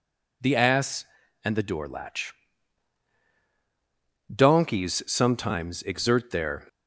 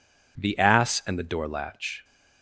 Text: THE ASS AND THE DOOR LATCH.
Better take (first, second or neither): second